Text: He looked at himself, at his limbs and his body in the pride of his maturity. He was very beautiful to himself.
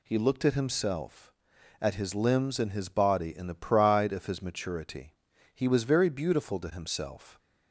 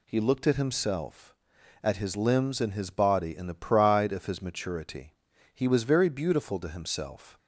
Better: neither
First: none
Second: none

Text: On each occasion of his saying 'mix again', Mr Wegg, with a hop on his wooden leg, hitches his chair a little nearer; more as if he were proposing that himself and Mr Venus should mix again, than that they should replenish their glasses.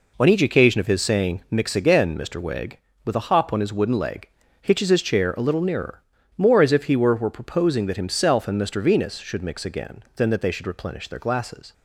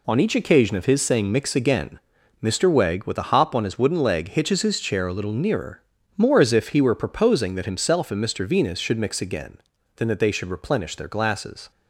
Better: second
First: says "were" twice; at 7.1 s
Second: none

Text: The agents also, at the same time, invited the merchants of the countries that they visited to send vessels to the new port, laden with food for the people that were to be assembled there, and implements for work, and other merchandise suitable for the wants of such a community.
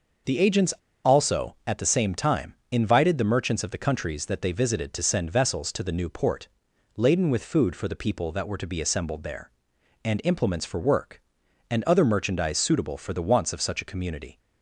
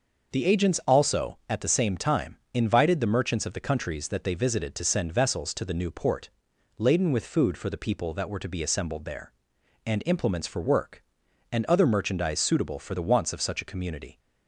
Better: second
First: pauses between "agents" and "also"; slight; at 0.7 s; 0.32 s long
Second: none

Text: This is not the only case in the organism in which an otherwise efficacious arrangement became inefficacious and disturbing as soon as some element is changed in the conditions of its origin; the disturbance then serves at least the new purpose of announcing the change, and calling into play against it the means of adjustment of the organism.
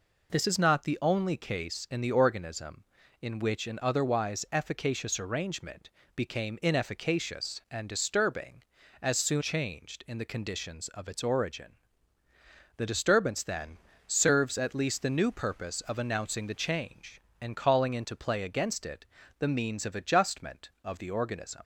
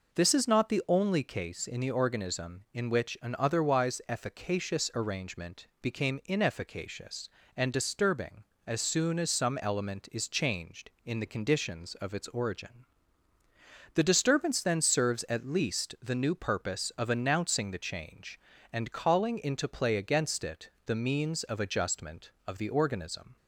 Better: second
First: pauses between "arrangement" and "became"; slight; at 5.8 s; 0.26 s long // skips "as some element is"; at 9.4 s // pauses between "then" and "serves"; slight; at 13.7 s; 0.28 s long // pauses between "it" and "the"; slight; at 19.0 s; 0.32 s long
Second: pauses between "it" and "the"; slight; at 20.6 s; 0.16 s long

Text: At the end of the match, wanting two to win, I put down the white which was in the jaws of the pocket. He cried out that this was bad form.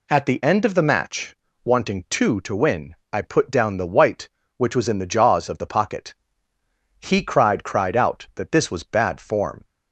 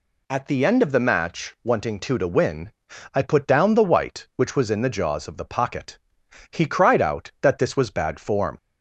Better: second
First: says "cried" twice; at 7.6 s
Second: none

